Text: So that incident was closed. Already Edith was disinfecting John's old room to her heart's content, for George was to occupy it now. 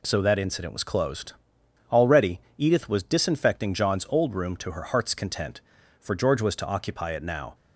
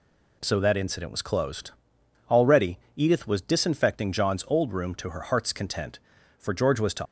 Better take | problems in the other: first | pauses between "Already" and "Edith"; slight; at 2.7 s; 0.16 s long; slight in the first // stops before "occupy it now"; at 7.0 s

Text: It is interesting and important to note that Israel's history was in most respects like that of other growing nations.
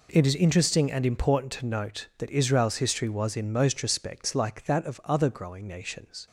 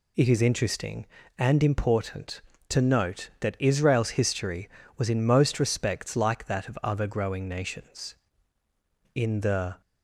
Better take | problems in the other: first | goes on to say "In the"; noticeable; from 9.1 s on; 0.66 s long

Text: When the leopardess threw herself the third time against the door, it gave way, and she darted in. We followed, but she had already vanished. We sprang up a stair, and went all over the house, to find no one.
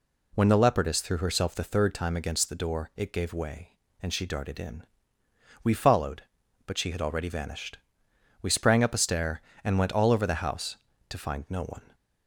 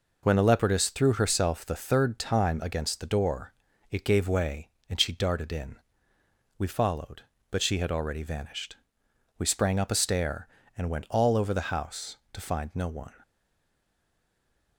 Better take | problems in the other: first | stays silent after the last word; noticeable; from 13.2 s on; 1.5 s long

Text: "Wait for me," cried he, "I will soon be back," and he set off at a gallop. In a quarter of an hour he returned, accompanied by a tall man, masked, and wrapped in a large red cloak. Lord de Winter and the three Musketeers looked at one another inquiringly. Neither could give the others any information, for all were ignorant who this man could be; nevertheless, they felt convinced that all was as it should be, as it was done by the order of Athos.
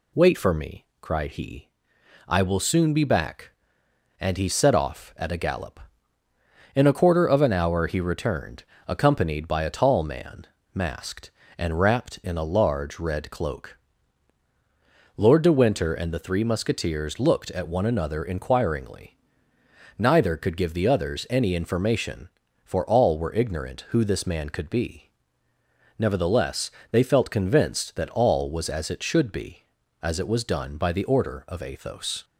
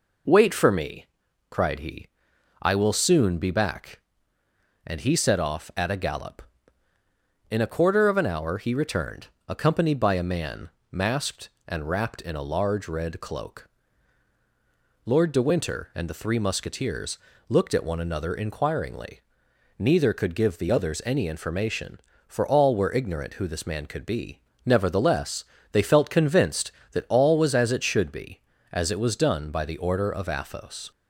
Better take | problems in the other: first | skips "tall"; at 10.2 s // pauses between "Musketeers" and "looked"; slight; at 17.1 s; 0.30 s long

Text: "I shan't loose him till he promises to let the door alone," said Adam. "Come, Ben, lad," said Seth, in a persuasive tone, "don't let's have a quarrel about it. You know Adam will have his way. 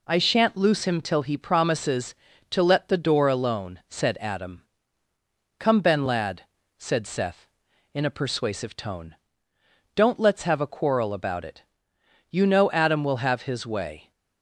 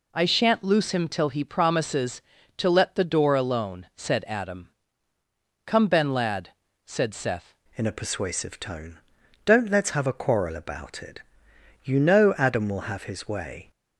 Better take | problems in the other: first | changes voice at "in"; from 7.7 s on; 6.0 s long

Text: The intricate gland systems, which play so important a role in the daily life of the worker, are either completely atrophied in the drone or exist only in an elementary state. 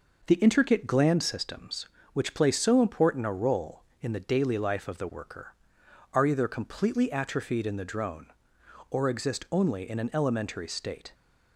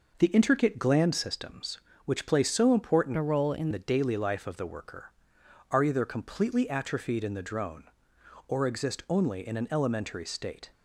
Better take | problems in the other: first | changes voice from "a" to "in"; from 3.1 to 3.6 s; 0.5 s long

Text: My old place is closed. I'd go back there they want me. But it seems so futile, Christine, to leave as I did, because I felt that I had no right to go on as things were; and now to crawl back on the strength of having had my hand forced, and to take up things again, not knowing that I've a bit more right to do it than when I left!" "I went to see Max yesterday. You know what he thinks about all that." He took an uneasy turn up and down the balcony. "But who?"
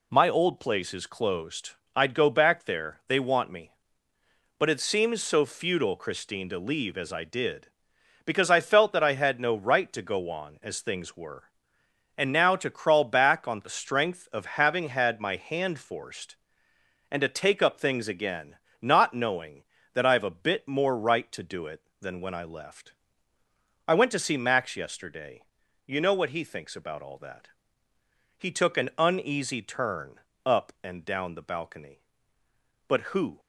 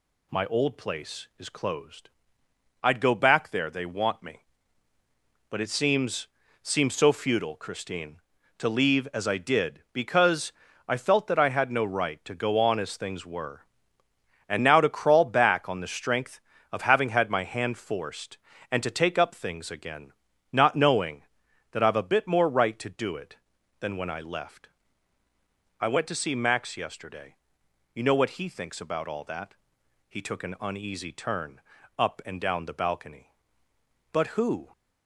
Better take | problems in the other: first | says "seems" twice; at 6.6 s // pauses between "because" and "I"; slight; at 10.5 s; 0.36 s long // pauses between "turn" and "up"; slight; at 31.5 s; 0.36 s long; slight in the first

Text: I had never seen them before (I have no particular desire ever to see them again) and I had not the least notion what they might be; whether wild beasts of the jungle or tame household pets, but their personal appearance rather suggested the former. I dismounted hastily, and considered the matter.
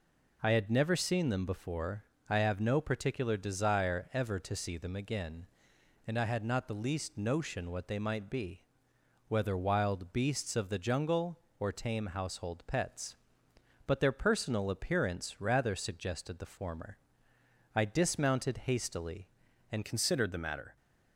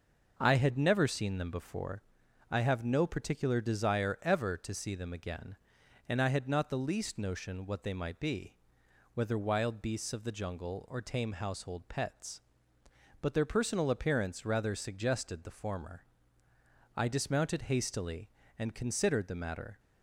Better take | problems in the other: second | changes voice at "considered"; from 19.8 s on; 0.9 s long

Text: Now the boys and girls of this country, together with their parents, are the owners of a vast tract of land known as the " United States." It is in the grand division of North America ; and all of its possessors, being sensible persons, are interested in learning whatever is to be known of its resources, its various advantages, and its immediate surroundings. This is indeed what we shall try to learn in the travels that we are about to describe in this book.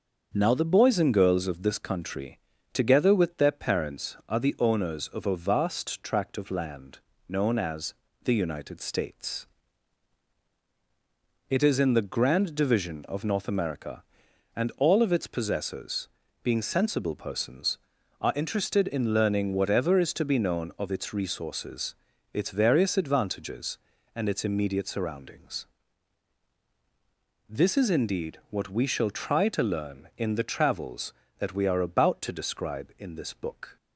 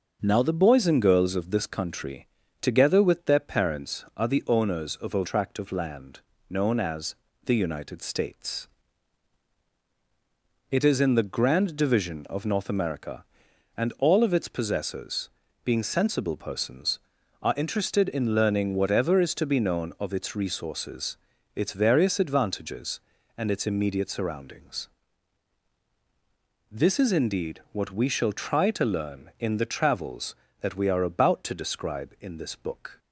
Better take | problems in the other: first | starts louder than the rest; until 1.2 s; 6 dB; also in the first // skips "vast"; at 5.2 s // pauses between "land" and "known"; slight; at 6.2 s; 0.28 s long; slight in the first // pauses between "as" and "the"; slight; at 7.1 s; 0.30 s long; slight in the first

